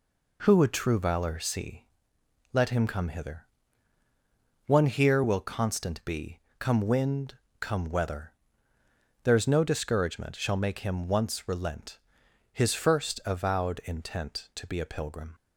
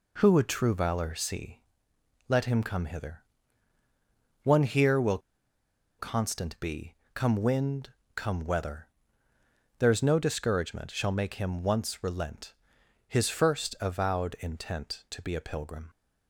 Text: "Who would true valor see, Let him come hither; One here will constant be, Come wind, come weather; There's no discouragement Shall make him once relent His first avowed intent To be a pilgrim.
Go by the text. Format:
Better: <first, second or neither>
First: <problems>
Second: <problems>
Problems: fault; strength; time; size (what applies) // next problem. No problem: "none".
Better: first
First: pauses between "relent" and "His"; noticeable; at 11.9 s; 0.54 s long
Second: pauses between "will" and "constant"; noticeable; at 5.1 s; 0.80 s long // pauses between "relent" and "His"; noticeable; at 12.5 s; 0.54 s long